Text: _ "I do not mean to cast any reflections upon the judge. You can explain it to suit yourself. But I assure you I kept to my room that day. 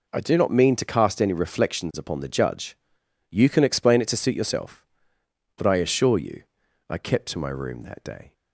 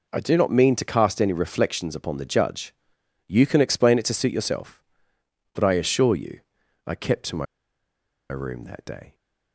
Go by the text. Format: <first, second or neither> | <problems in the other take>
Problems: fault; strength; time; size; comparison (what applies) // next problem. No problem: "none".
first | pauses between "you" and "I"; noticeable; at 6.3 s; 0.46 s long; noticeable in the first // pauses between "my" and "room"; noticeable; at 7.4 s; 0.86 s long